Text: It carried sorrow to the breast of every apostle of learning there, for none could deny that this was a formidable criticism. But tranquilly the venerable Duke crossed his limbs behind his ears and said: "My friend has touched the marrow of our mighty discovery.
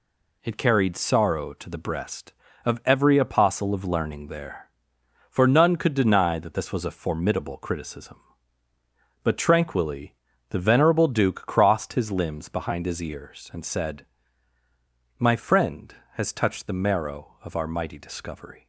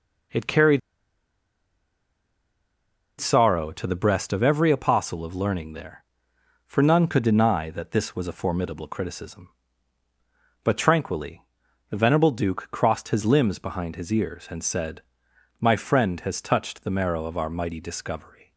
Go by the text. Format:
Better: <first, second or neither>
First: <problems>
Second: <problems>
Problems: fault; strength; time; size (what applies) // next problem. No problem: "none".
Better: first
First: pauses between "tranquilly" and "the"; slight; at 10.1 s; 0.34 s long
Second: pauses between "carried" and "sorrow"; strong; at 0.7 s; 2.3 s long // pauses between "tranquilly" and "the"; noticeable; at 11.4 s; 0.48 s long